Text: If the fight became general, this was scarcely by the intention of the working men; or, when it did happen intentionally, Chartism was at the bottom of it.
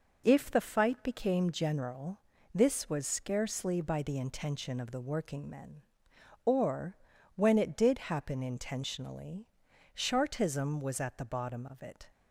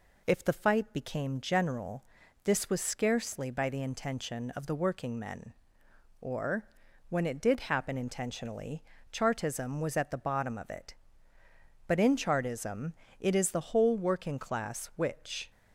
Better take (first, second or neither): first